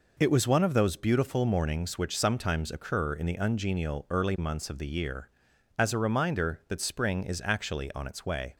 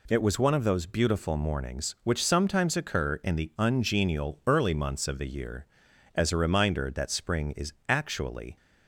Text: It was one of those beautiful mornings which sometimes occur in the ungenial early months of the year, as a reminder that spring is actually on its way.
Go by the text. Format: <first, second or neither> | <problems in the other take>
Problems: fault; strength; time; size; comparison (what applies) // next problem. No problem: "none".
first | stops before "on its way"; at 8.5 s